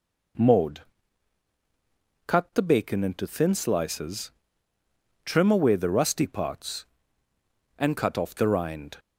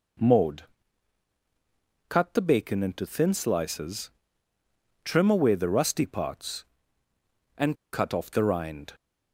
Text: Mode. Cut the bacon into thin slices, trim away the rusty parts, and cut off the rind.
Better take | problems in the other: first | pauses between "and" and "cut"; slight; at 7.7 s; 0.16 s long

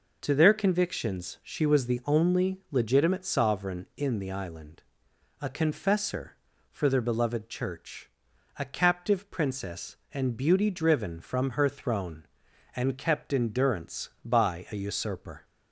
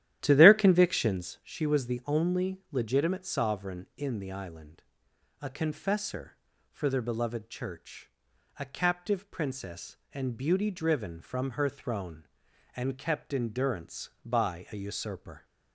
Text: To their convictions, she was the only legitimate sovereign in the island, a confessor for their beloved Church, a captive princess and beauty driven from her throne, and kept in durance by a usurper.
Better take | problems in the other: first | starts louder than the rest; strong; until 1.4 s; 12.5 dB

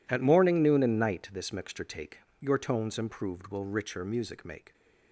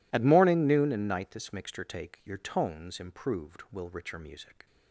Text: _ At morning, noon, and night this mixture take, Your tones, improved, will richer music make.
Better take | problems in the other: first | stops before "make"; at 4.6 s

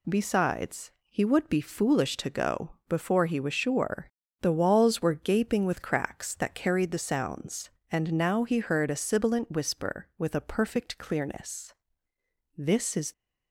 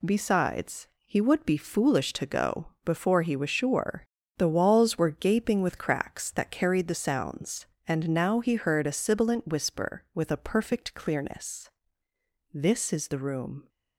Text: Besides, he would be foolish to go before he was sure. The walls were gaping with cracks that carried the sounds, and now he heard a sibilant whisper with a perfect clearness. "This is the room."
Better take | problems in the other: second | pauses between "go" and "before"; slight; at 2.7 s; 0.16 s long; slight in the second // stops before "the room"; at 13.1 s

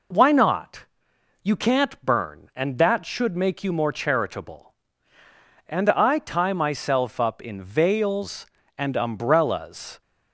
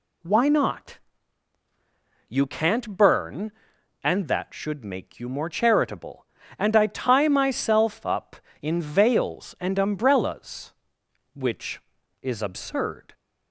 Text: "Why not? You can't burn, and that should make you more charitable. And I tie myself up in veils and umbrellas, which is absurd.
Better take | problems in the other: second | stops before "which is absurd"; at 10.0 s

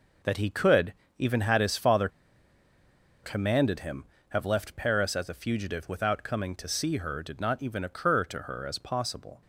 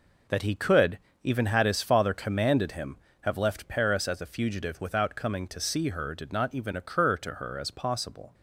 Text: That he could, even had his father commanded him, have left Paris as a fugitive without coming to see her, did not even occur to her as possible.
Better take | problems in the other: second | pauses between "father" and "commanded"; at 2.0 s; 1.1 s long

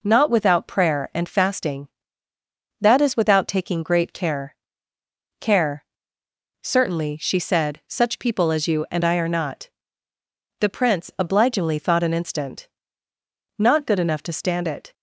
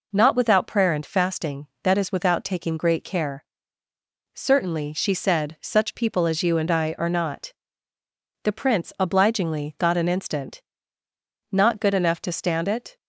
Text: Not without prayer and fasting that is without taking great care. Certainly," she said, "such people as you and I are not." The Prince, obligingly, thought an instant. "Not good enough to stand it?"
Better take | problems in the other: second | says "care" twice; at 5.3 s

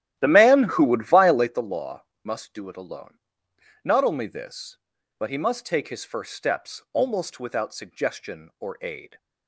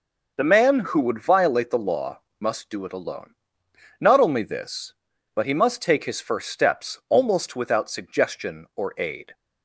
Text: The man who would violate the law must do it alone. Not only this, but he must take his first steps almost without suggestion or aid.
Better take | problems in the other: second | starts louder than the rest; strong; until 1.7 s; 12.5 dB // pauses between "law" and "must"; slight; at 2.0 s; 0.18 s long; slight in the second

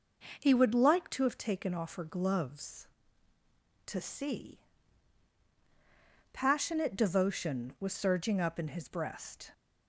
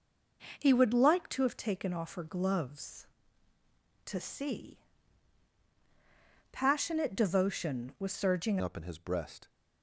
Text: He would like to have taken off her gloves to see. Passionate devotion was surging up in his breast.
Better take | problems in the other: first | changes voice at "up"; from 8.6 s on; 0.8 s long

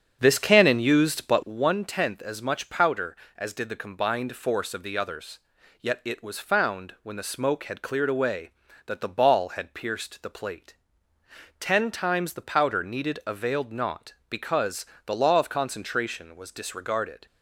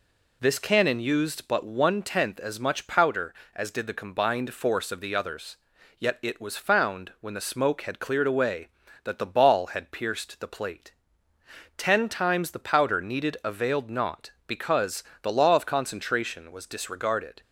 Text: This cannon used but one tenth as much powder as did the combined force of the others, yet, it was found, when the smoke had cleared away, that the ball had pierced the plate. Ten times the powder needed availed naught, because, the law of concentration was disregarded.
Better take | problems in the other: second | starts louder than the rest; strong; until 1.6 s; 7.5 dB

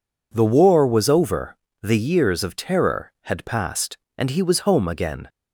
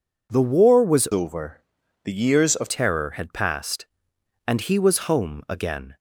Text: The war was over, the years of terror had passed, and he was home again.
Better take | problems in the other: first | changes voice from "over" to "of"; from 1.1 to 2.6 s; 1.5 s long

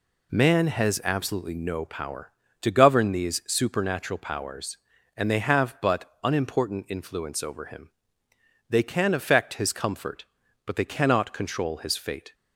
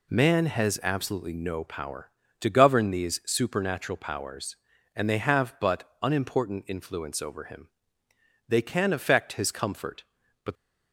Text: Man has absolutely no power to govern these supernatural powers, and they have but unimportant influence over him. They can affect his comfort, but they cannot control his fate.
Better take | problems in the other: first | stops before "they cannot control his fate"; at 10.5 s

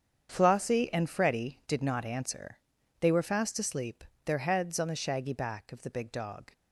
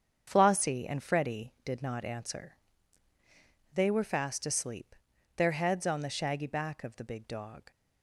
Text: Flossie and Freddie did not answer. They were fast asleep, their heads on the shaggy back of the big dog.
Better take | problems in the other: neither | starts louder than the rest; strong; the same in both

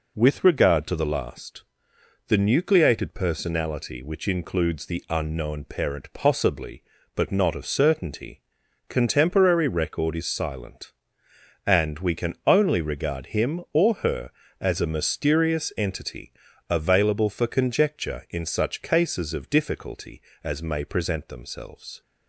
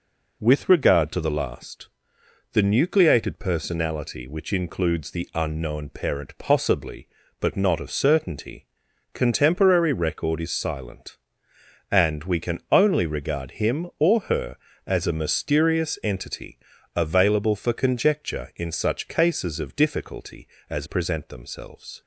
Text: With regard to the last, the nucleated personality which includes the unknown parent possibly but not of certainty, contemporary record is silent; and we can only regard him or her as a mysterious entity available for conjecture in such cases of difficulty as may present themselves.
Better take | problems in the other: first | pauses between "entity" and "available"; at 16.5 s; 0.38 s long; also in the first // skips "may"; at 20.8 s

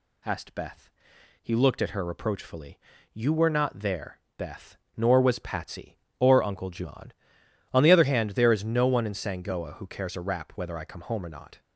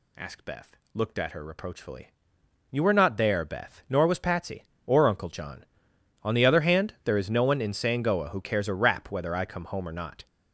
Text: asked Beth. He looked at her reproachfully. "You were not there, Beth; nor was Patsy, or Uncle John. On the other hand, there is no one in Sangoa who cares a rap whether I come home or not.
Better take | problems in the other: first | skips "He"; at 0.8 s

